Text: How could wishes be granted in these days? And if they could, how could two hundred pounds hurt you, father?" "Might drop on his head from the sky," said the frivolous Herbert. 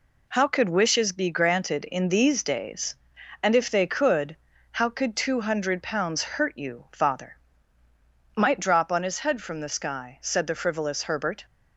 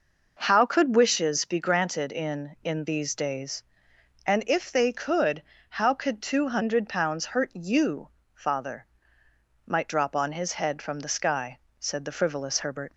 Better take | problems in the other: first | says "in" twice; at 2.6 s

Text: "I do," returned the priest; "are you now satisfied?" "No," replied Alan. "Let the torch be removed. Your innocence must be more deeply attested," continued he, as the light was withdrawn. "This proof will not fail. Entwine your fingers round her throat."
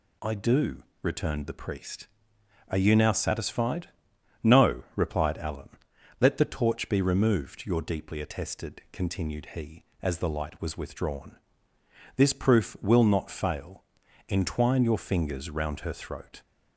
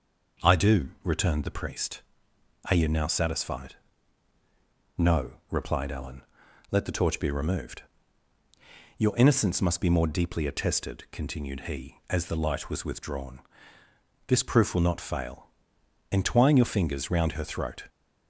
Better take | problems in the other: second | skips "innocence must be more"; at 7.8 s

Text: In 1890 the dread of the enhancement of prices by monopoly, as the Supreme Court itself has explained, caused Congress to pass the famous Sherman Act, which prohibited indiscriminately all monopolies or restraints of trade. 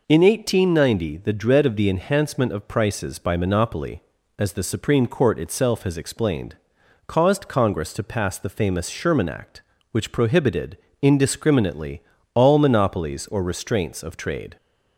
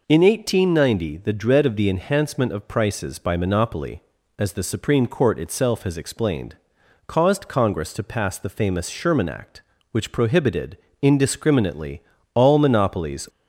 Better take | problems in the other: first | pauses between "prohibited" and "indiscriminately"; slight; at 10.7 s; 0.24 s long; slight in the first // pauses between "indiscriminately" and "all"; slight; at 12.0 s; 0.32 s long; slight in the first // stops before "or restraints of trade"; at 13.2 s

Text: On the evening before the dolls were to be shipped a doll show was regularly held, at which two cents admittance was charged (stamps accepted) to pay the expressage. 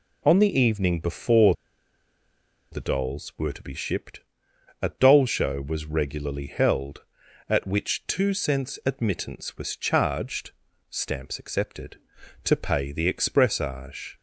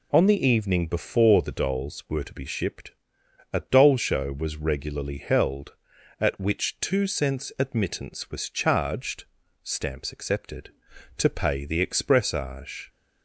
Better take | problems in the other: second | pauses between "before" and "the"; at 1.5 s; 1.1 s long // pauses between "shipped" and "a"; noticeable; at 4.1 s; 0.62 s long; noticeable in the second

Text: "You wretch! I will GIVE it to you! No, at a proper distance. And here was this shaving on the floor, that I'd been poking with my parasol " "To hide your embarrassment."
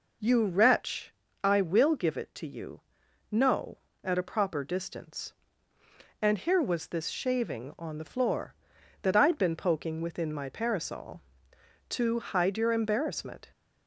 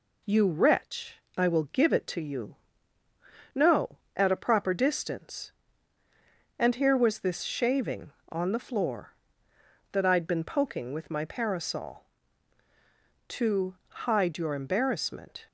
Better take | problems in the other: second | says "within" for "with"; at 10.0 s

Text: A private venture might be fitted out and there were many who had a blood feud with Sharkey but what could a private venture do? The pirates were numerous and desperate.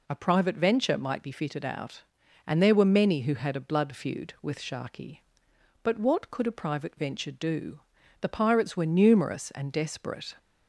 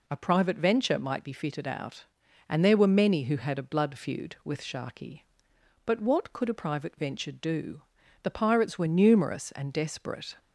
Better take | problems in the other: neither | none

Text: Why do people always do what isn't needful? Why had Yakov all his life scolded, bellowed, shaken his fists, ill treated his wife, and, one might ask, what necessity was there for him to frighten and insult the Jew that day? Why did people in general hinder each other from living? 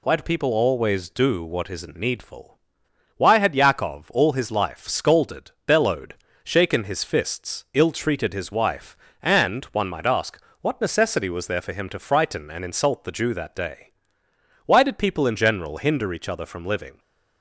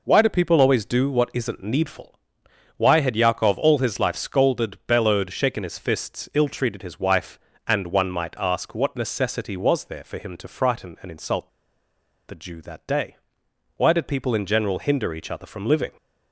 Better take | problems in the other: first | pauses between "insult" and "the"; noticeable; at 11.4 s; 0.78 s long

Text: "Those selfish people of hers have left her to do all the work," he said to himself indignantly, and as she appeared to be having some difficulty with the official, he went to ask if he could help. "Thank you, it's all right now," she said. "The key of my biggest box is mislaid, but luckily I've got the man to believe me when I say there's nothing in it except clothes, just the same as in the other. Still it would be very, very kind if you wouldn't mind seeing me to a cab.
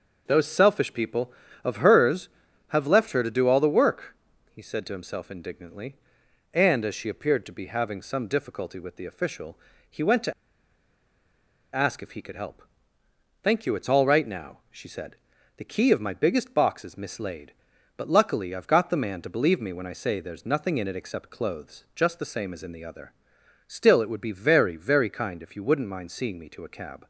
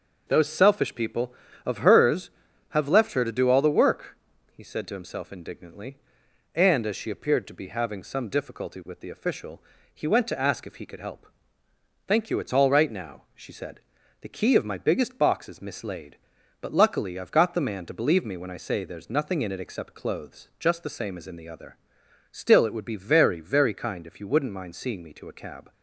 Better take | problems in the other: second | starts louder than the rest; until 1.2 s; 6.5 dB; also in the second // pauses between "to" and "ask"; strong; at 10.3 s; 1.4 s long

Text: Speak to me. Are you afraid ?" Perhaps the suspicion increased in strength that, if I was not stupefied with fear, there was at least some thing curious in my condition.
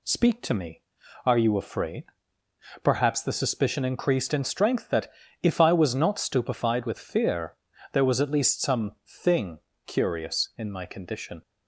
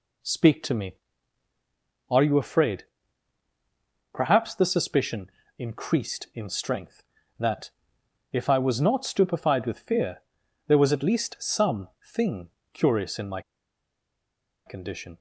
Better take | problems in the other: first | pauses between "suspicion" and "increased"; slight; at 5.3 s; 0.26 s long // pauses between "some" and "thing"; slight; at 11.8 s; 0.18 s long // pauses between "thing" and "curious"; slight; at 12.4 s; 0.24 s long; slight in the first // pauses between "my" and "condition"; strong; at 13.4 s; 1.2 s long

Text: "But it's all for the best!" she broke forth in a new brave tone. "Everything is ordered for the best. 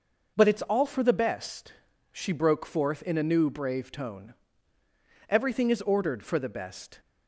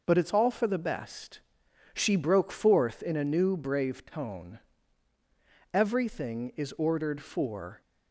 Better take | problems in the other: first | stops before "the best"; at 7.8 s

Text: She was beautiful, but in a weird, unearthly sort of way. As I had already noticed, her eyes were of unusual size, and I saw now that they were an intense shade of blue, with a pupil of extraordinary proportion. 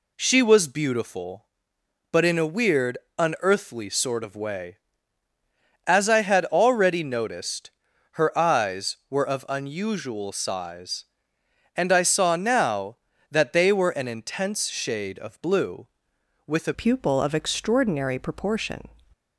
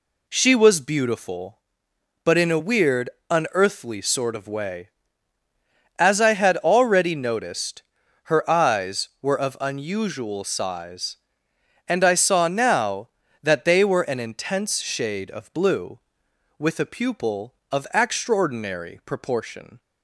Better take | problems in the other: second | changes voice at "pupil"; from 16.7 s on; 2.1 s long

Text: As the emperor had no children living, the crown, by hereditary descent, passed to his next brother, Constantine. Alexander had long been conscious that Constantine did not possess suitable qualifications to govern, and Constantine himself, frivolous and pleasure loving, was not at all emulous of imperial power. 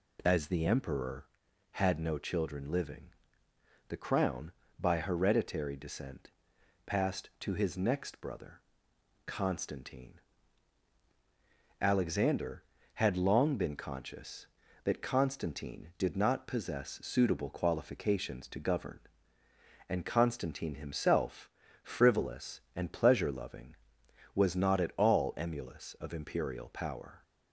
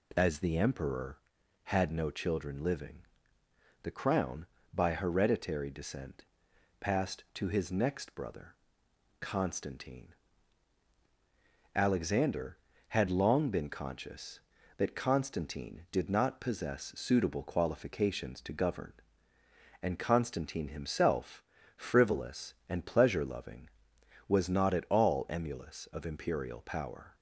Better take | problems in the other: neither | none

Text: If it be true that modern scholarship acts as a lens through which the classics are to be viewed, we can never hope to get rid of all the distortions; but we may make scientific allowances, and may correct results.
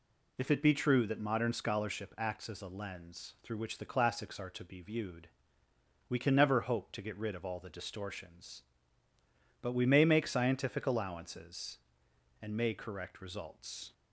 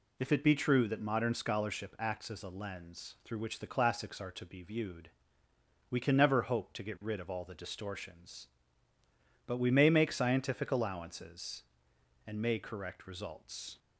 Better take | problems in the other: neither | none

